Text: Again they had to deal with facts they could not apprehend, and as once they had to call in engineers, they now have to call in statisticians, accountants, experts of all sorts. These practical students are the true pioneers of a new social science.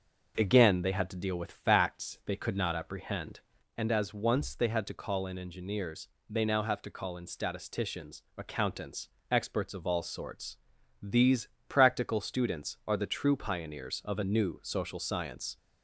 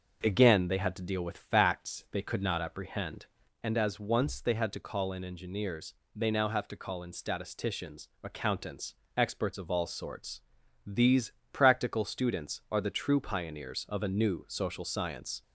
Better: neither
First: pauses between "These" and "practical"; slight; at 11.4 s; 0.22 s long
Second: pauses between "These" and "practical"; slight; at 11.3 s; 0.22 s long

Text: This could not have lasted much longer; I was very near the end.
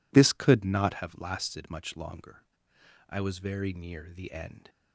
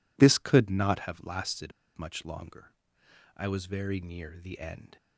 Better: first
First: none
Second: pauses between "lasted" and "much"; slight; at 1.7 s; 0.25 s long

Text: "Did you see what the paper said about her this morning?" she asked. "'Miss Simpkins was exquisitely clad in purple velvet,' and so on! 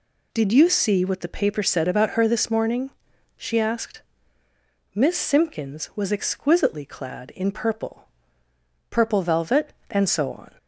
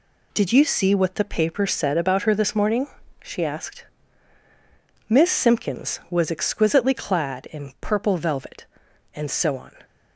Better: second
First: says "purple" twice; at 8.9 s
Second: none

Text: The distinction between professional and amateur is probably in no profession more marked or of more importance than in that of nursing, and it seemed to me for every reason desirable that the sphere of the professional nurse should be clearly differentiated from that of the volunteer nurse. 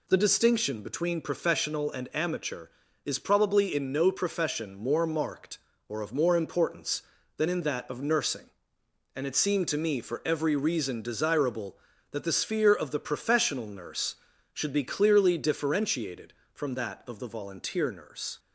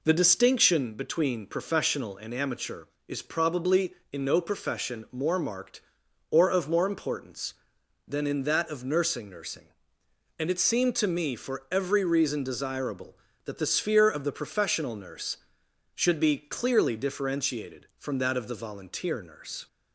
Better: first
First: none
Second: says "nursing" twice; at 9.2 s

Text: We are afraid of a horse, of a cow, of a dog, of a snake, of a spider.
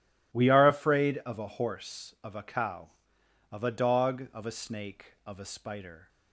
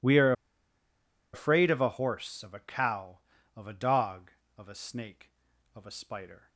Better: first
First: none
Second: pauses between "are" and "afraid"; at 0.3 s; 1.0 s long

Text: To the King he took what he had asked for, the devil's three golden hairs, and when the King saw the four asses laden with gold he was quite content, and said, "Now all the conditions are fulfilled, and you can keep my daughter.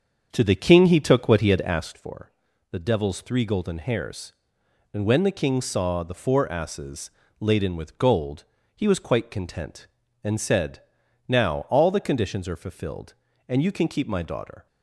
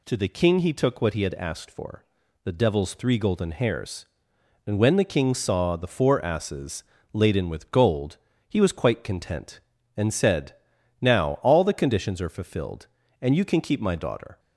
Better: second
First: starts louder than the rest; strong; until 2.0 s; 7 dB // pauses between "asses" and "laden"; slight; at 7.1 s; 0.30 s long // pauses between "gold" and "he"; slight; at 8.4 s; 0.32 s long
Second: pauses between "asses" and "laden"; slight; at 6.8 s; 0.30 s long // pauses between "gold" and "he"; slight; at 8.1 s; 0.32 s long

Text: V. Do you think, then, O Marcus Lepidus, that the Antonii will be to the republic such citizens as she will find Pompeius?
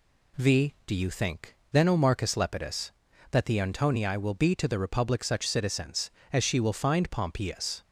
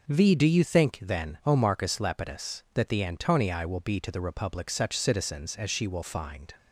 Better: first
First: none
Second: stops before "Pompeius"; at 6.5 s

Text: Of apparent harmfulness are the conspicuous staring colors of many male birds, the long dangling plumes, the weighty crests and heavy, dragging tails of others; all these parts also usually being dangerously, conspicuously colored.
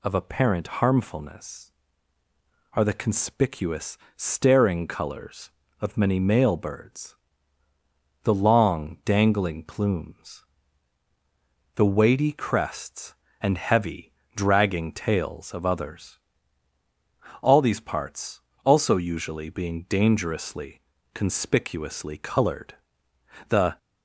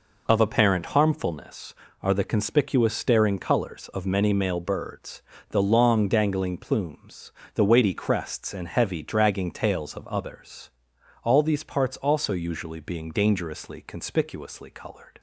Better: second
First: pauses between "conspicuous" and "staring"; slight; at 3.9 s; 0.18 s long // pauses between "parts" and "also"; slight; at 18.3 s; 0.24 s long // goes on to say "The"; slight; from 23.4 s on; 0.28 s long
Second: none

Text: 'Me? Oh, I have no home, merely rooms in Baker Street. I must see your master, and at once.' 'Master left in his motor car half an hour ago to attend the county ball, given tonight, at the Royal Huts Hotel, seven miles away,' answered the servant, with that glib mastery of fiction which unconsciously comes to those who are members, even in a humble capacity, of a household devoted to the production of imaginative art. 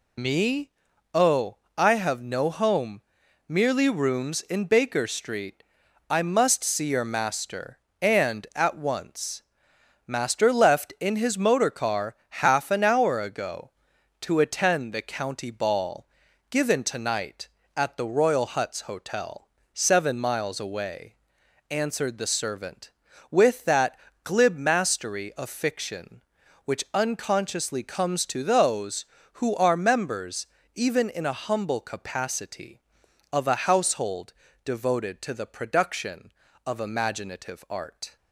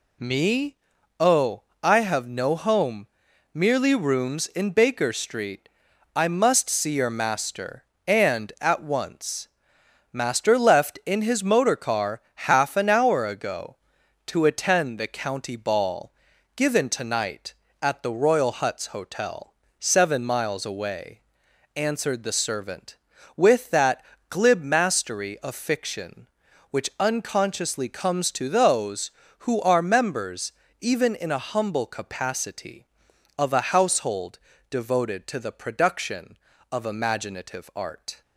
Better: second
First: loses the start of "Me"; at 0.1 s; 30 ms // pauses between "car" and "half"; slight; at 12.1 s; 0.30 s long // pauses between "that" and "glib"; slight; at 23.9 s; 0.24 s long // pauses between "household" and "devoted"; slight; at 34.3 s; 0.32 s long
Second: pauses between "car" and "half"; slight; at 12.1 s; 0.30 s long // pauses between "that" and "glib"; slight; at 24.0 s; 0.24 s long // pauses between "household" and "devoted"; slight; at 34.3 s; 0.32 s long

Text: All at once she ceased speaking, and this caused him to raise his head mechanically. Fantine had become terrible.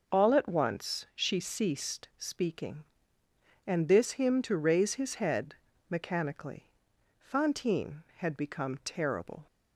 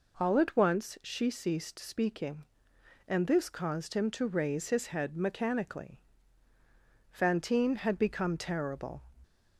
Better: second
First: skips "caused"; at 4.1 s // pauses between "head" and "mechanically"; slight; at 5.5 s; 0.34 s long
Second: none

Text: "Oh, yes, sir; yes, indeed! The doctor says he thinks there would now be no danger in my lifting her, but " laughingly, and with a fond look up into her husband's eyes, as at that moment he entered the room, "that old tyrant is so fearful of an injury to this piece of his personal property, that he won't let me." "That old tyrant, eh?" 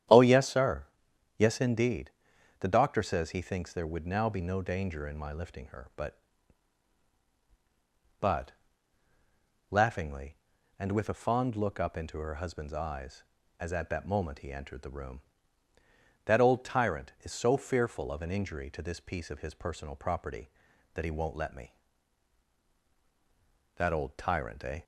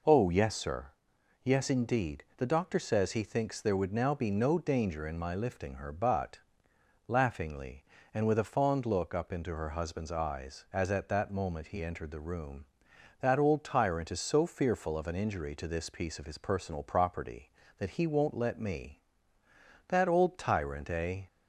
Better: second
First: starts louder than the rest; strong; until 1.6 s; 10 dB // says "but" twice; at 8.2 s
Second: none

